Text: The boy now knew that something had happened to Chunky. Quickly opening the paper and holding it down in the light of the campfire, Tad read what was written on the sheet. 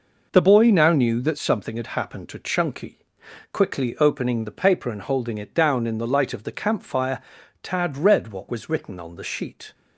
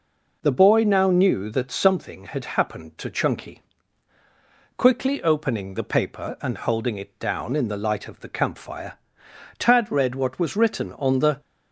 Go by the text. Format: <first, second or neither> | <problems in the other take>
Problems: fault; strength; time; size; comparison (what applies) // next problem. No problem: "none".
first | stops before "sheet"; at 11.3 s